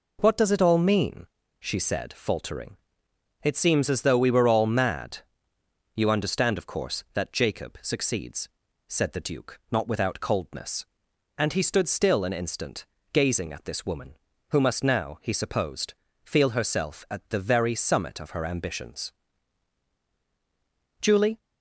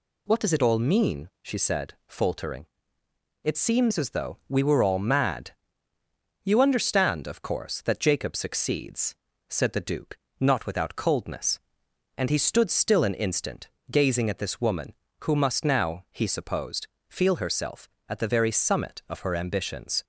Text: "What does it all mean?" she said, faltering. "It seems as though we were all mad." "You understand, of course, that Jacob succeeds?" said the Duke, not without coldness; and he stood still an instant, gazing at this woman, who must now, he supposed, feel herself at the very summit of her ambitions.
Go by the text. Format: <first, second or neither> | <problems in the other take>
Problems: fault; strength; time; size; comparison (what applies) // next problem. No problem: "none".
second | goes on to say "Julie"; slight; from 21.0 s on; 0.38 s long